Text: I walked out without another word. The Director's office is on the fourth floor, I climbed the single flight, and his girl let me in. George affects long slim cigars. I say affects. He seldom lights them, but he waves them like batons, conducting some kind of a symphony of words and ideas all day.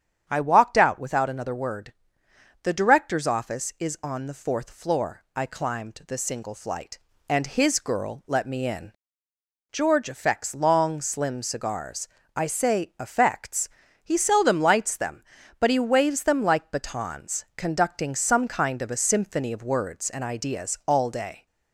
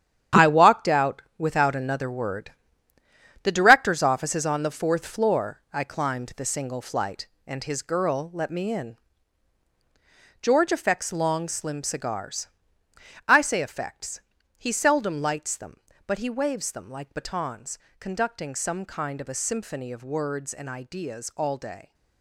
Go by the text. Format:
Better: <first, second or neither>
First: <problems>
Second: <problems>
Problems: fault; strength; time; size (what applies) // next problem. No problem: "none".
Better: first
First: starts louder than the rest; strong; until 1.2 s; 8.5 dB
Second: gets quieter; strong; throughout; 10 dB // starts louder than the rest; strong; until 1.5 s; 9.5 dB // pauses between "out" and "without"; slight; at 1.2 s; 0.16 s long